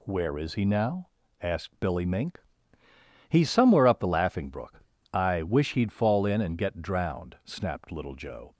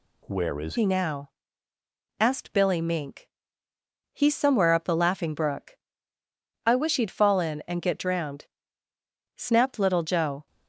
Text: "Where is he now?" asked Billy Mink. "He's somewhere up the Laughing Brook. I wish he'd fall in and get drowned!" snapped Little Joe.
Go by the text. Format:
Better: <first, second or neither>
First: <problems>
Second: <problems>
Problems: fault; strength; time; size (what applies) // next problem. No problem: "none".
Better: first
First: none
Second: changes voice at "he"; from 0.7 s on; 9.7 s long